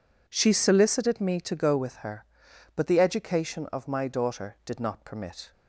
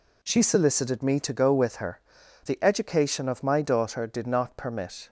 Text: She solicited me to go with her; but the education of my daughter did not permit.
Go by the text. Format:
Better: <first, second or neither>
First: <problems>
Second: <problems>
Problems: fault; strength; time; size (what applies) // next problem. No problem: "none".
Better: first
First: none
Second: skips "but"; at 2.2 s